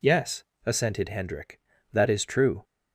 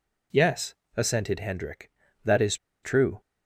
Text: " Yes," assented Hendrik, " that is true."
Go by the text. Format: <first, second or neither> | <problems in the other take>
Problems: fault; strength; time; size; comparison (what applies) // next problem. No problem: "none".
first | pauses between "is" and "true"; slight; at 2.5 s; 0.27 s long